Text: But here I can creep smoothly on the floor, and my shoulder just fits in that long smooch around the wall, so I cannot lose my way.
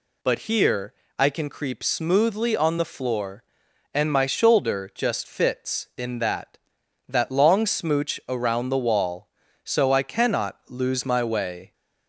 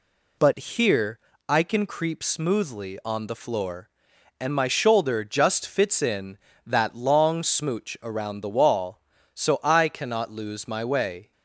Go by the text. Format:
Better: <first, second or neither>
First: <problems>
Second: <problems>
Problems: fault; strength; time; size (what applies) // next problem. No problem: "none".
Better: second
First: pauses between "here" and "I"; slight; at 0.9 s; 0.24 s long // says "that" twice; at 7.1 s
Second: pauses between "here" and "I"; slight; at 1.1 s; 0.28 s long